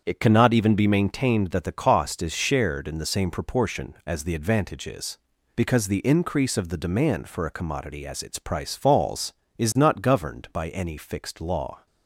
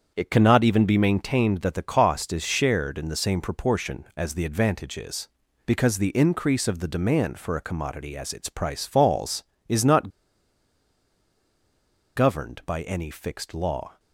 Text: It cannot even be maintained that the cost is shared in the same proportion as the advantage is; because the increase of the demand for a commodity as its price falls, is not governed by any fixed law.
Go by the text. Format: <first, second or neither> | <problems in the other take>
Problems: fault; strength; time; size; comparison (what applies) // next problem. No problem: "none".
first | starts louder than the rest; strong; until 1.1 s; 7.5 dB; strong in the first // pauses between "not" and "governed"; strong; at 10.0 s; 2.0 s long